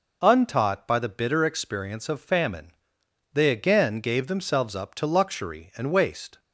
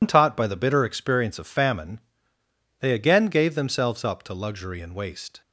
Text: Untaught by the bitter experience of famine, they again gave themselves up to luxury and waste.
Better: first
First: none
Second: loses the start of "Untaught"; at 0.0 s; 130 ms

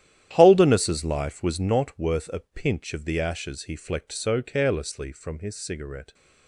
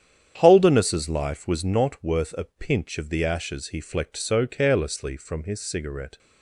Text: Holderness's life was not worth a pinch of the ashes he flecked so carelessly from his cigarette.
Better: second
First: gets quieter; strong; throughout; 13 dB // starts louder than the rest; strong; until 1.3 s; 11.5 dB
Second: starts louder than the rest; strong; until 1.4 s; 9 dB

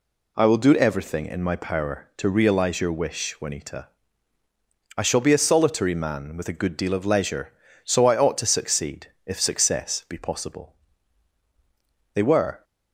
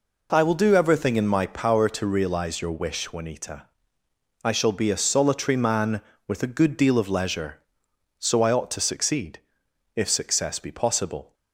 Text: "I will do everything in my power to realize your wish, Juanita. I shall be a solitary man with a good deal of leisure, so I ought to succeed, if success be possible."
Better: second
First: goes on to say "They were"; slight; from 12.1 s on; 0.48 s long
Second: none

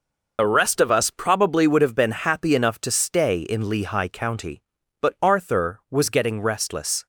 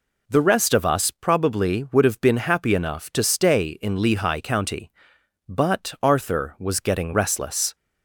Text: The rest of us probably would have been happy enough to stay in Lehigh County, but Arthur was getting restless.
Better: second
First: loses the start of "The"; at 0.3 s; 60 ms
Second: none

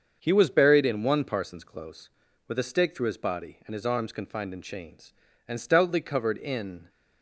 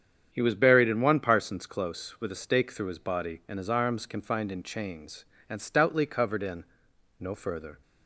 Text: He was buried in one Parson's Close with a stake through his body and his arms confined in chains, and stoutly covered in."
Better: first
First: starts louder than the rest; until 1.2 s; 6.5 dB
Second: starts louder than the rest; strong; until 1.3 s; 8.5 dB // goes on to say "No further"; noticeable; from 7.1 s on; 0.62 s long

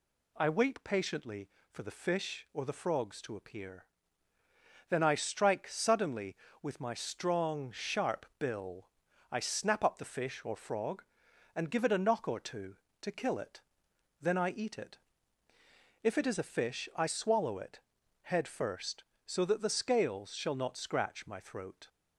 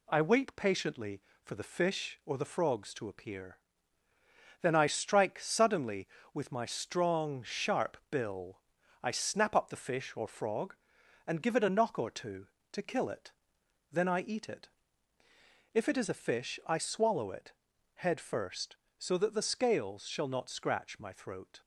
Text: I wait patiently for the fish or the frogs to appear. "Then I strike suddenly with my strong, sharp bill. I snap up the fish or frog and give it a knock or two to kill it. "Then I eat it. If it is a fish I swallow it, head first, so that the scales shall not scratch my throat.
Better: first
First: none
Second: gets quieter; slight; throughout; 2.5 dB

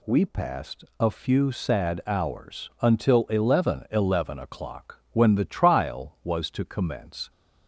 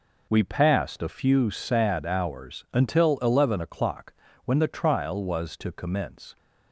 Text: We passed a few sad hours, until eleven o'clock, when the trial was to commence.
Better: second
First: pauses between "passed" and "a"; slight; at 0.8 s; 0.16 s long // says "eleven" twice; at 3.9 s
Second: none

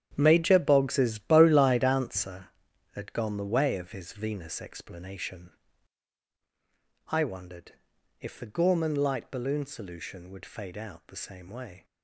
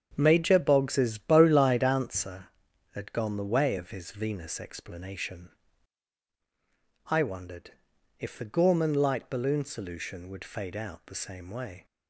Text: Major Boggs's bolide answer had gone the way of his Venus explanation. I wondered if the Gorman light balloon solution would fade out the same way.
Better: second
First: gets quieter; strong; throughout; 12 dB // starts louder than the rest; strong; until 1.1 s; 9.5 dB // pauses between "wondered" and "if"; noticeable; at 7.7 s; 0.48 s long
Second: starts louder than the rest; strong; until 1.1 s; 7.5 dB // pauses between "wondered" and "if"; noticeable; at 7.7 s; 0.48 s long

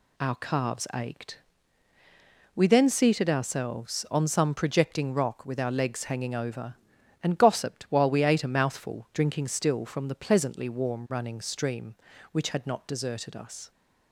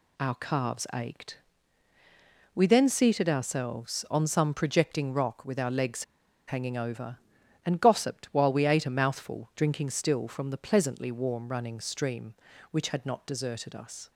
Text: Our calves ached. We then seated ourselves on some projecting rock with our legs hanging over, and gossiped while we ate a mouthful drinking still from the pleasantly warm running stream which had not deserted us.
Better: first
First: none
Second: pauses between "legs" and "hanging"; at 6.0 s; 0.44 s long

